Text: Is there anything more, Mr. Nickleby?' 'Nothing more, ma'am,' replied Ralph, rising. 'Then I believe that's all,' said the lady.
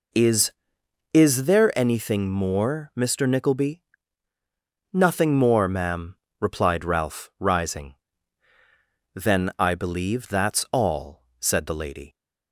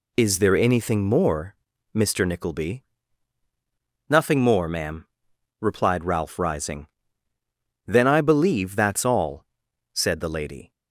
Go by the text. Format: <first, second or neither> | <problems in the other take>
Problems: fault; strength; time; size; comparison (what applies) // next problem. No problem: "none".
second | says "Is" twice; at 1.1 s